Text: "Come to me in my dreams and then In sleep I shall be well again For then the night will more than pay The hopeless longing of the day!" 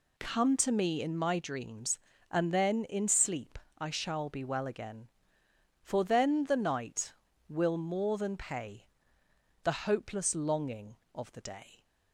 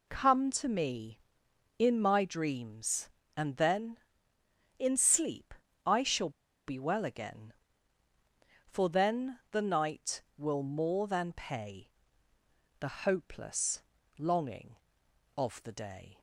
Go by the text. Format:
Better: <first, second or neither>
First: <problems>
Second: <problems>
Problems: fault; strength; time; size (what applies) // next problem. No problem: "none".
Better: first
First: pauses between "sleep" and "I"; slight; at 3.5 s; 0.18 s long // pauses between "pay" and "The"; noticeable; at 8.8 s; 0.78 s long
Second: pauses between "sleep" and "I"; slight; at 5.5 s; 0.32 s long // pauses between "shall" and "be"; at 6.2 s; 0.37 s long // pauses between "pay" and "The"; noticeable; at 11.8 s; 0.90 s long // pauses between "hopeless" and "longing"; slight; at 13.8 s; 0.36 s long